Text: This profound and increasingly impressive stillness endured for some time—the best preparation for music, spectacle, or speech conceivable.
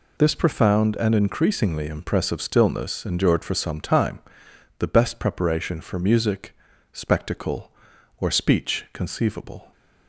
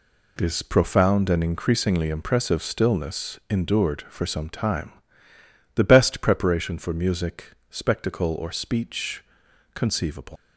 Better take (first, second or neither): first